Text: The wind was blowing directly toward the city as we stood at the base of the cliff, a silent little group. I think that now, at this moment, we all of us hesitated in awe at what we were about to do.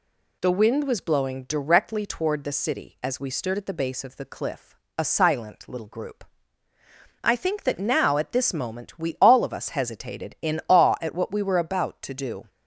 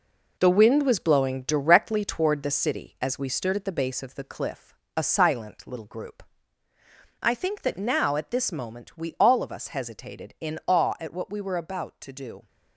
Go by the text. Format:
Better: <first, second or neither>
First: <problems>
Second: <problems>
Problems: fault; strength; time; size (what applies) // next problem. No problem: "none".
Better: first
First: none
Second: gets quieter; strong; throughout; 8 dB